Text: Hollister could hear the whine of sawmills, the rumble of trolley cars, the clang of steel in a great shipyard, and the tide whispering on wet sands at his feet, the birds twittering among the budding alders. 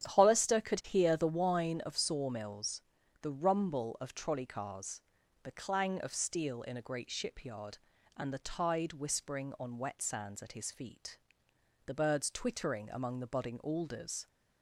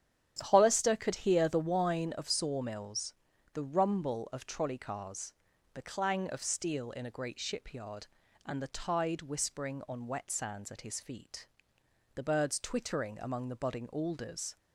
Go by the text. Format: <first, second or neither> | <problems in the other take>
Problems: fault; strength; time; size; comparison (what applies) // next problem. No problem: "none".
neither | starts louder than the rest; strong; the same in both